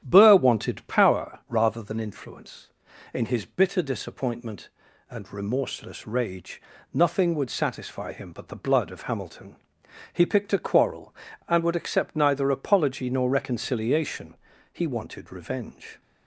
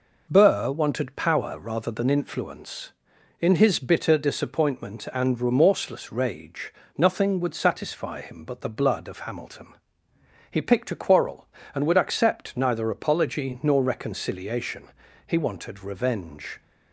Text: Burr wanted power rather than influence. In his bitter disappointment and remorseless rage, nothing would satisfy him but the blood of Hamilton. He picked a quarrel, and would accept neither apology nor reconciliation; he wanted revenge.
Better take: second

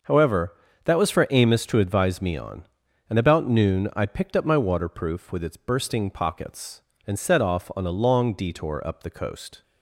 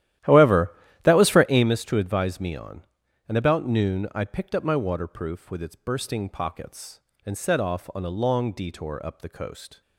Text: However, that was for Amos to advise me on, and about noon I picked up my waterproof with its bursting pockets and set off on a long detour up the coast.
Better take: first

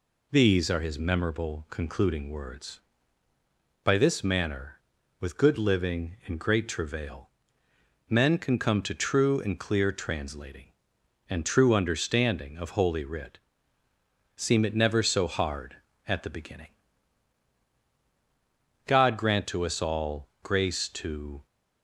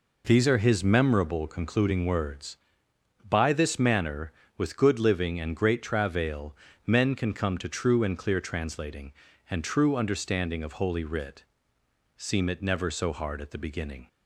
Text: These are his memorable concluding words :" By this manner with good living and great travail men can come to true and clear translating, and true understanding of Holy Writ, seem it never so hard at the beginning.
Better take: second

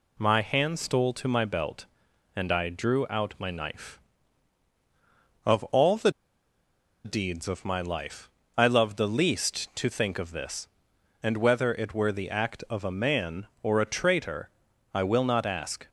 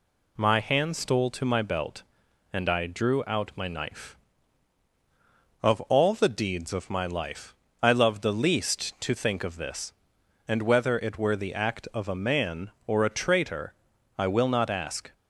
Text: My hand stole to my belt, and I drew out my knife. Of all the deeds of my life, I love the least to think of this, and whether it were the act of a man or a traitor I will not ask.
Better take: second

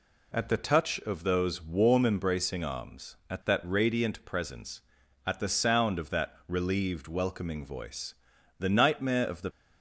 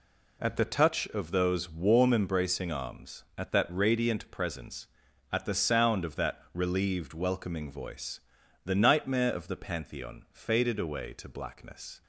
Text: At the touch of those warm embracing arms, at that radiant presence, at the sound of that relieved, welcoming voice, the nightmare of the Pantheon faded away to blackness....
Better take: second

